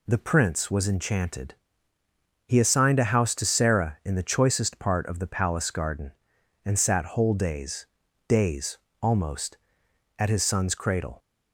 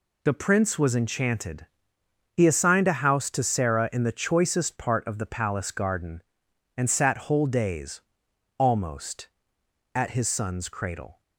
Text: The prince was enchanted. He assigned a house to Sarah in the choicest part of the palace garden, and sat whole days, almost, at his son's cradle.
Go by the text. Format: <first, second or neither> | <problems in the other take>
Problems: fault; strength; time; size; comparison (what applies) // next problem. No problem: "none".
second | says "days" twice; at 8.2 s